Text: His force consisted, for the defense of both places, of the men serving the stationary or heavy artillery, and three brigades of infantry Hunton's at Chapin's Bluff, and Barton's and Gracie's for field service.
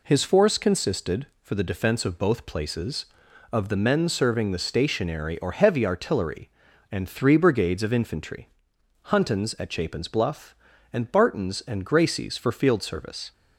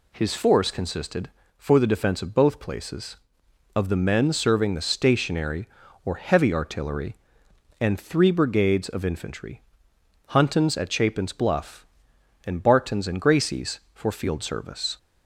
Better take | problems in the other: neither | pauses between "infantry" and "Hunton's"; noticeable; the same in both

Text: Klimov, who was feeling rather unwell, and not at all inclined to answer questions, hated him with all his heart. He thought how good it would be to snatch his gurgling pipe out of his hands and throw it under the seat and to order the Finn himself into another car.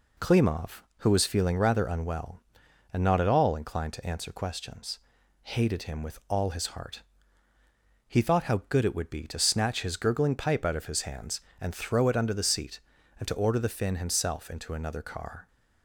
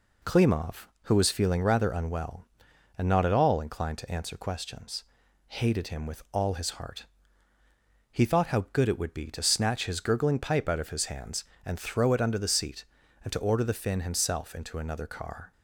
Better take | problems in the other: neither | none

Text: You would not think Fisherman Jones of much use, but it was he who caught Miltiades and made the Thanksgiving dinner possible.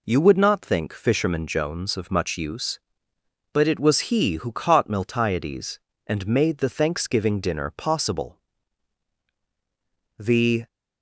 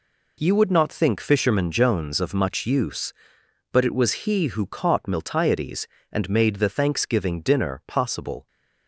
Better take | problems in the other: second | goes on to say "The"; slight; from 10.1 s on; 0.48 s long

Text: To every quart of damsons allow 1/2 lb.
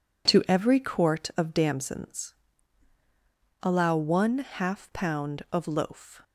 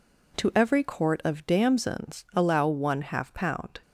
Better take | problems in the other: second | pauses between "damsons" and "allow"; strong; at 2.3 s; 1.2 s long // goes on to say "of loaf"; noticeable; from 5.5 s on; 0.70 s long

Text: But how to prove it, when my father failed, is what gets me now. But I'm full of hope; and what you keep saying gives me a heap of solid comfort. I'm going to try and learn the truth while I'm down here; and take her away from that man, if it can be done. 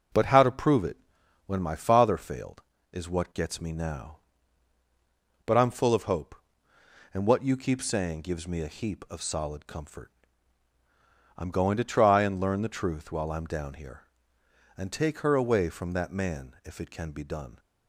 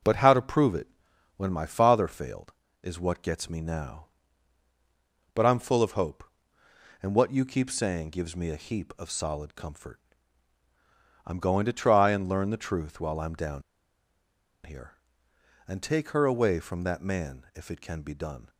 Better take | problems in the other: first | pauses between "down" and "here"; at 13.6 s; 1.0 s long

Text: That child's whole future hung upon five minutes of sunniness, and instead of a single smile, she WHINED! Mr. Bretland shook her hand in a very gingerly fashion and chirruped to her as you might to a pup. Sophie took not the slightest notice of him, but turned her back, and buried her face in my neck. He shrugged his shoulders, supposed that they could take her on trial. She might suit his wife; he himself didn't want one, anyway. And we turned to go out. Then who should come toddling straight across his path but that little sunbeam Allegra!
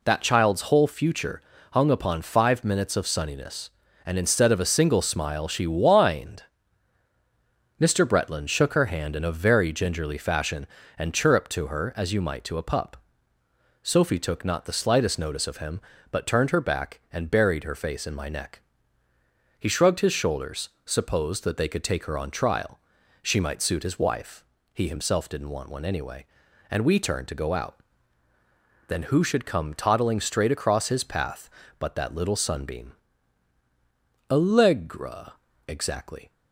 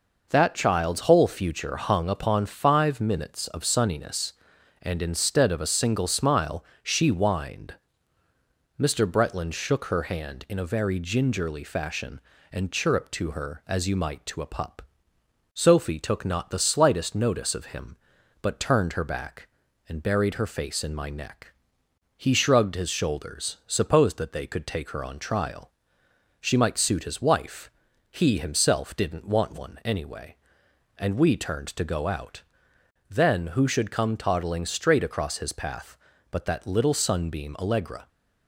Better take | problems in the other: second | pauses between "future" and "hung"; slight; at 1.3 s; 0.32 s long // pauses between "sunbeam" and "Allegra"; strong; at 32.9 s; 1.3 s long // goes on to say "Exactly"; noticeable; from 35.6 s on; 0.64 s long

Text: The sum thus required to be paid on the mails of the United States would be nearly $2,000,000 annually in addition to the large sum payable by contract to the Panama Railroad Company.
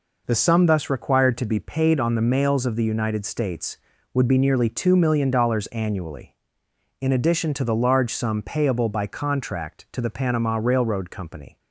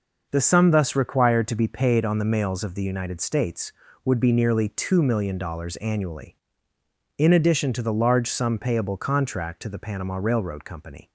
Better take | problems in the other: first | skips "by"; at 8.9 s

